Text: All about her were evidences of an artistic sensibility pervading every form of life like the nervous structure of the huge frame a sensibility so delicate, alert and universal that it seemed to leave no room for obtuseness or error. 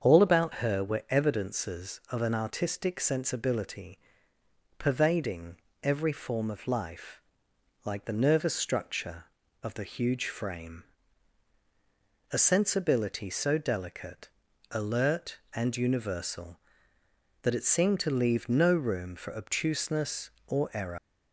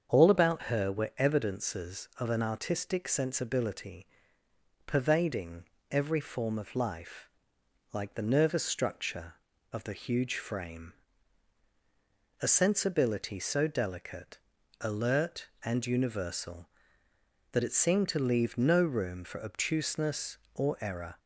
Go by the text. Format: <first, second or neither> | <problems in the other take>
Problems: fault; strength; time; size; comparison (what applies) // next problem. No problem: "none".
second | starts louder than the rest; until 1.0 s; 7 dB; strong in the second // pauses between "sensibility" and "pervading"; noticeable; at 3.9 s; 0.78 s long; noticeable in the second // pauses between "pervading" and "every"; slight; at 5.5 s; 0.26 s long; slight in the second // pauses between "life" and "like"; noticeable; at 7.2 s; 0.64 s long; noticeable in the second // pauses between "frame" and "a"; strong; at 10.8 s; 1.5 s long; strong in the second // leaves "error" unfinished; at 20.9 s; 125 ms